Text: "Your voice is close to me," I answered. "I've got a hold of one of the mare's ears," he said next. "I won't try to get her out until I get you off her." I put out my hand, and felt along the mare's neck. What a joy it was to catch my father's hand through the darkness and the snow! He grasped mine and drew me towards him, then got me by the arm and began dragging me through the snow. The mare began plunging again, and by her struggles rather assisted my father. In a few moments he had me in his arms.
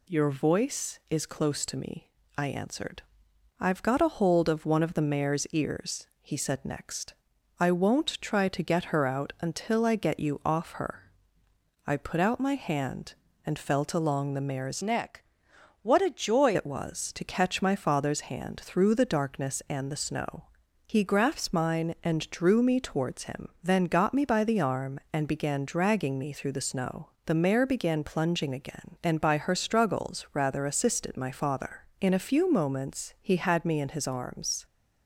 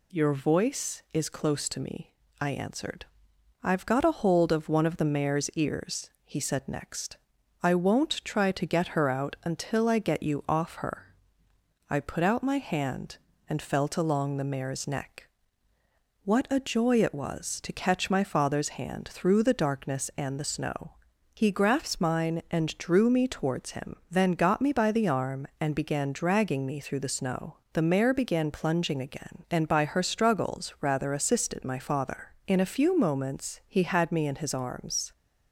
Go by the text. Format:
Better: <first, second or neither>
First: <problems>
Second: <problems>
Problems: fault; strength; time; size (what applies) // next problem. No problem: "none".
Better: second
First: changes voice from "neck" to "joy"; from 14.8 to 16.5 s; 1.7 s long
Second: none